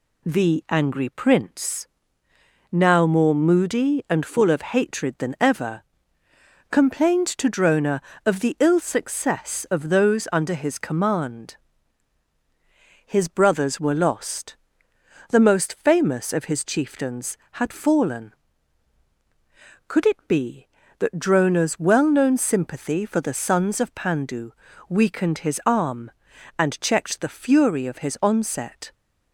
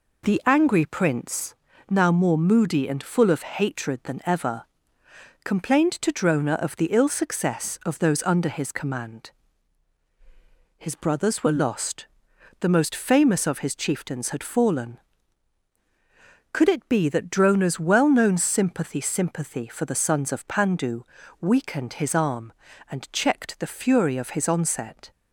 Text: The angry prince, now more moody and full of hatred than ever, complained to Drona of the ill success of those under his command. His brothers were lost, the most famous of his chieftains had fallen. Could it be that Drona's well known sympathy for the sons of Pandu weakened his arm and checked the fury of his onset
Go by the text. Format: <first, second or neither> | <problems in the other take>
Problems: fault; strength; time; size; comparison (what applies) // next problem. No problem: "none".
first | says "sympathy" twice; at 19.0 s // pauses between "Pandu" and "weakened"; at 21.0 s; 0.40 s long; slight in the first